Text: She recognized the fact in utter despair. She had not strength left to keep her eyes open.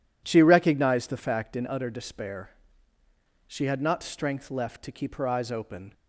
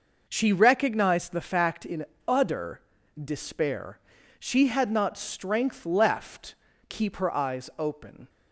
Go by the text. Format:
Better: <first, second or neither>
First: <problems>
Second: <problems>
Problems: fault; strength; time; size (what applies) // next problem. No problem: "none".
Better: first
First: none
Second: pauses between "in" and "utter"; slight; at 2.0 s; 0.22 s long // pauses between "utter" and "despair"; at 2.8 s; 0.40 s long // skips "to"; at 6.7 s